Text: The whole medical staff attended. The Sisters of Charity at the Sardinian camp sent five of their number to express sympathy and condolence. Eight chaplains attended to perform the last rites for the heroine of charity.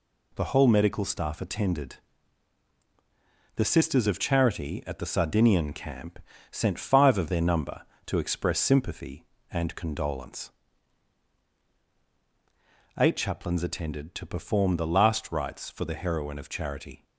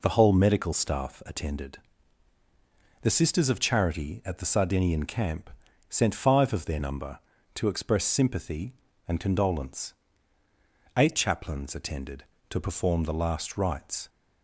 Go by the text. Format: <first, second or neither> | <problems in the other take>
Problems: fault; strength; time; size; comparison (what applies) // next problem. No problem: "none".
first | pauses between "camp" and "sent"; at 5.5 s; 0.38 s long; slight in the first // stops before "for the heroine of charity"; at 14.0 s